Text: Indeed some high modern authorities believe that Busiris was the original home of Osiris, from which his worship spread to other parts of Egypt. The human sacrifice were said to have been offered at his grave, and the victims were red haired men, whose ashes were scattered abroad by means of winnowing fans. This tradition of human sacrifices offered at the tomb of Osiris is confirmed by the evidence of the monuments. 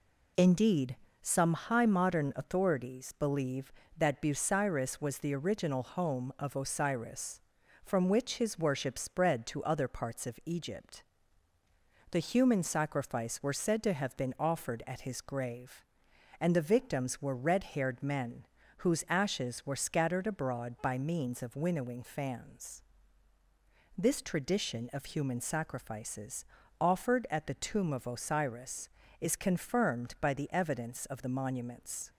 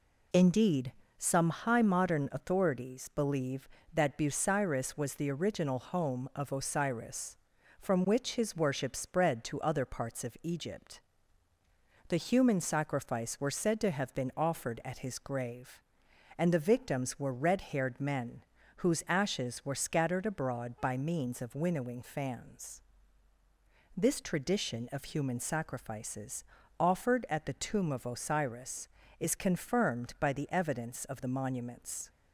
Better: neither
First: pauses between "Indeed" and "some"; slight; at 0.9 s; 0.24 s long // pauses between "sacrifices" and "offered"; slight; at 26.4 s; 0.36 s long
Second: pauses between "Indeed" and "some"; slight; at 0.9 s; 0.24 s long // pauses between "sacrifices" and "offered"; slight; at 26.4 s; 0.36 s long

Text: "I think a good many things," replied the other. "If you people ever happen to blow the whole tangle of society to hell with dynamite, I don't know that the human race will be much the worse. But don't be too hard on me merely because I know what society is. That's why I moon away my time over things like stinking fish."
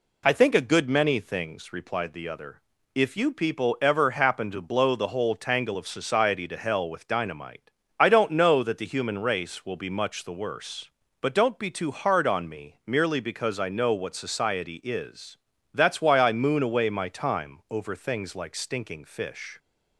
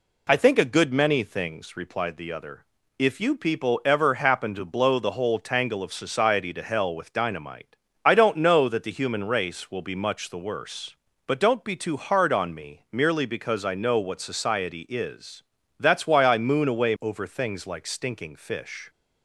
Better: first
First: none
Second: skips "my time"; at 16.9 s

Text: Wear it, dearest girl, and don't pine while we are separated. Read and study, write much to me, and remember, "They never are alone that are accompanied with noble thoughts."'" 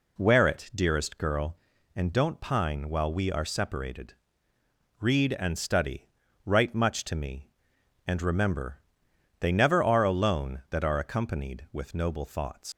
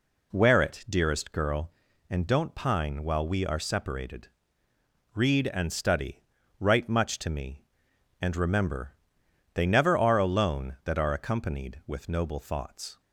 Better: second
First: leaves "thoughts" unfinished; at 12.7 s; 140 ms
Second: none

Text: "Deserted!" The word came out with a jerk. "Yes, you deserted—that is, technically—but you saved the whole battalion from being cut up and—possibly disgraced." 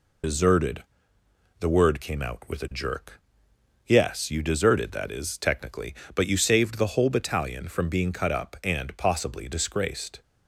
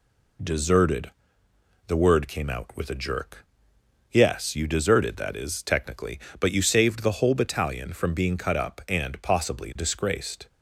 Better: second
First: loses the start of "Deserted"; at 0.2 s; 120 ms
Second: none

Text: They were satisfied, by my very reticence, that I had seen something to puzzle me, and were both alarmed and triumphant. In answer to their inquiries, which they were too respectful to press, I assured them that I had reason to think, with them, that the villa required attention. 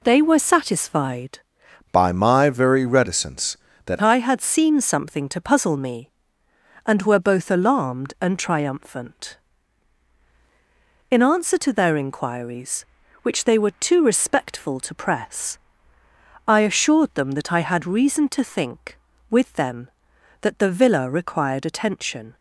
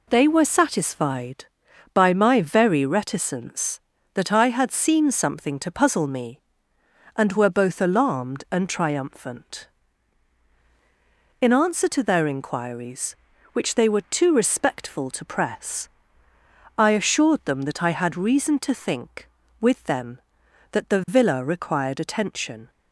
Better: second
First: changes voice from "by" to "that"; from 1.9 to 4.0 s; 2.1 s long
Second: none

